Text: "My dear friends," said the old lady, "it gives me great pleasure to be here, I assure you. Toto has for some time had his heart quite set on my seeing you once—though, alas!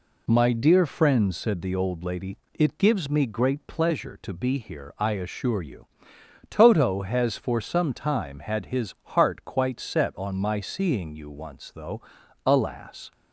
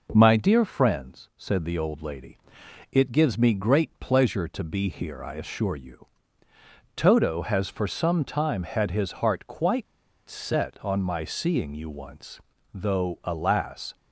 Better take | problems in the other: first | pauses between "quite" and "set"; at 9.8 s; 0.43 s long

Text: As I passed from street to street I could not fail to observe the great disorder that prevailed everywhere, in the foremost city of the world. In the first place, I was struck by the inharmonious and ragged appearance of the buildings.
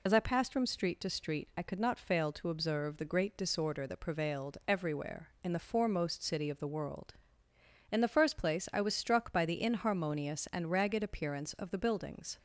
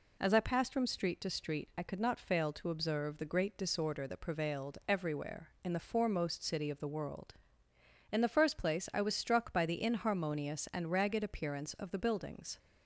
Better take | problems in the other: second | loses the start of "As"; at 0.0 s; 60 ms

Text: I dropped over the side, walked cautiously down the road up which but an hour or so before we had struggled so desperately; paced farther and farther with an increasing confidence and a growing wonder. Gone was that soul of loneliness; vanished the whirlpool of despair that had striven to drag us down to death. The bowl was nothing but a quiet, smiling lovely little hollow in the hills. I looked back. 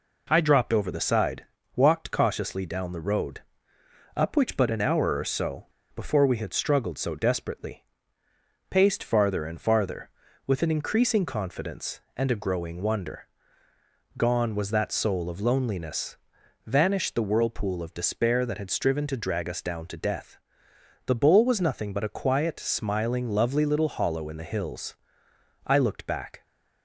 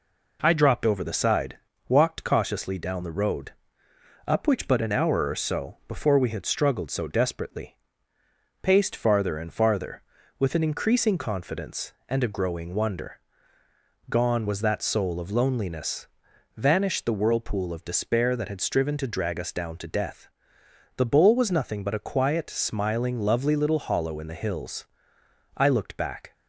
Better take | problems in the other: second | pauses between "road" and "up"; noticeable; at 3.4 s; 0.76 s long; noticeable in the second // pauses between "so" and "before"; slight; at 5.6 s; 0.28 s long

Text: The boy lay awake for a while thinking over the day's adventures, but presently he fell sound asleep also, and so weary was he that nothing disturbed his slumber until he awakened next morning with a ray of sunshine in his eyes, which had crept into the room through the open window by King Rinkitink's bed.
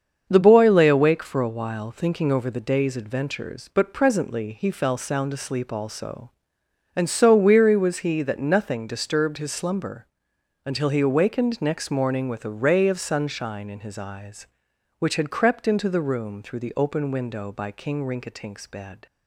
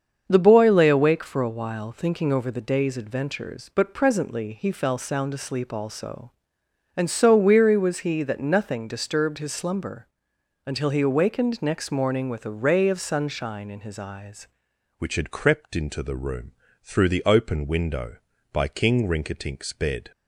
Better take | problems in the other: first | starts louder than the rest; until 1.2 s; 7 dB; also in the first // pauses between "slumber" and "until"; noticeable; at 10.0 s; 0.56 s long; noticeable in the first // changes voice at "which"; from 14.9 s on; 5.2 s long // pauses between "room" and "through"; slight; at 16.5 s; 0.30 s long

